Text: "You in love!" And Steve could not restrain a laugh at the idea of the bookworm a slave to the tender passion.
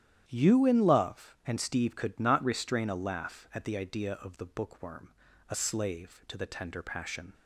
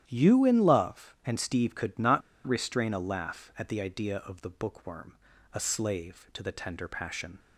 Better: first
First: starts louder than the rest; strong; until 1.2 s; 11 dB // pauses between "bookworm" and "a"; at 5.1 s; 0.38 s long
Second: starts louder than the rest; strong; until 1.0 s; 11 dB // pauses between "not" and "restrain"; slight; at 2.2 s; 0.25 s long // pauses between "bookworm" and "a"; at 5.1 s; 0.38 s long

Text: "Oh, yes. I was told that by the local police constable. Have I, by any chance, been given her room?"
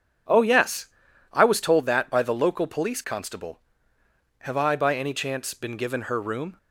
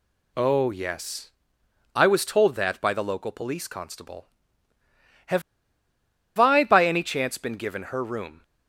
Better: first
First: none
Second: pauses between "Have" and "I"; noticeable; at 5.4 s; 0.96 s long

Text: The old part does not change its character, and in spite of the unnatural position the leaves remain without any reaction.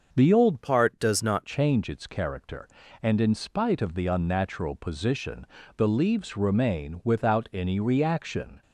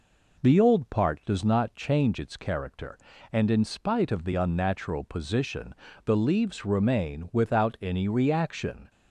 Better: second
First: starts louder than the rest; until 1.1 s; 6.5 dB // changes voice from "part" to "not"; from 0.6 to 1.4 s; 0.8 s long // pauses between "position" and "the"; slight; at 5.4 s; 0.30 s long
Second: pauses between "position" and "the"; slight; at 5.7 s; 0.30 s long

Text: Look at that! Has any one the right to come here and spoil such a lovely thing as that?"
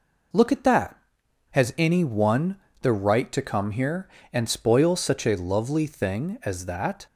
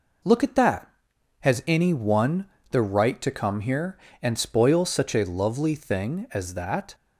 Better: neither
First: pauses between "one" and "the"; slight; at 2.5 s; 0.26 s long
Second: pauses between "one" and "the"; slight; at 2.4 s; 0.26 s long

